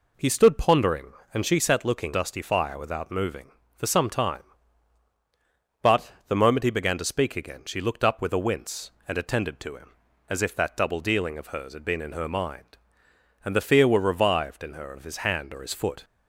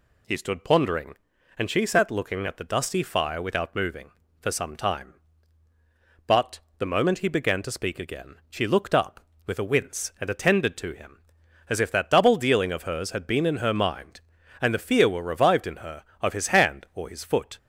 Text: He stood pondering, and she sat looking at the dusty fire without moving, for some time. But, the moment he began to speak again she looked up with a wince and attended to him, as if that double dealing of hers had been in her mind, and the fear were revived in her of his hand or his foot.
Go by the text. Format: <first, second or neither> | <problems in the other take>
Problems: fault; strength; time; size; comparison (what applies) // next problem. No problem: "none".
second | skips "at the"; at 2.1 s